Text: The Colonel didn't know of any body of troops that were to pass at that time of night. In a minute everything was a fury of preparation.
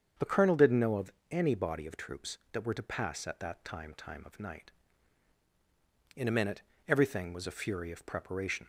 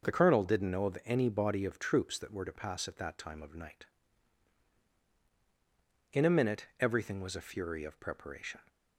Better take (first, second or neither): second